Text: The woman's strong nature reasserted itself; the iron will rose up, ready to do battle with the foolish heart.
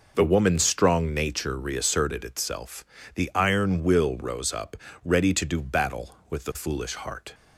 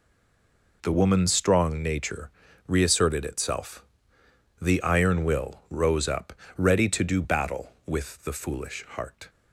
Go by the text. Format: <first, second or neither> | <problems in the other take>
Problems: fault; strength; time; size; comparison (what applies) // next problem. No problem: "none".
first | stays silent before the first word; slight; until 0.8 s; 0.8 s long // pauses between "nature" and "reasserted"; at 2.2 s; 0.38 s long